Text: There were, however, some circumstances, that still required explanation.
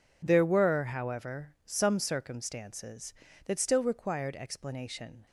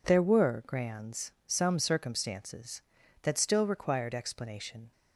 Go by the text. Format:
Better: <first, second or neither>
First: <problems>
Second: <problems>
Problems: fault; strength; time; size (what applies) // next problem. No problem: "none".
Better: first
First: none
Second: says "grands" for "however"; at 0.6 s